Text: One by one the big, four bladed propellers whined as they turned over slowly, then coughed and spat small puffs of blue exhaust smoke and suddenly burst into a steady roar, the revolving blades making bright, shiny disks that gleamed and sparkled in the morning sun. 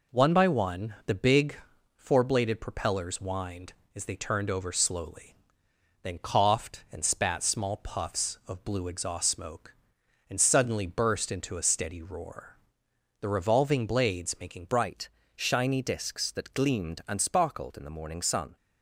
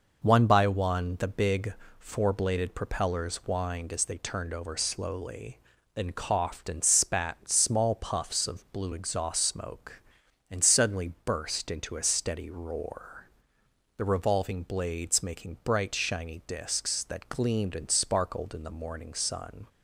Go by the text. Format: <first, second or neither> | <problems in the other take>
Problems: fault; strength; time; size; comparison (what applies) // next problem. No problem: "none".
second | changes voice at "bright"; from 14.6 s on; 3.9 s long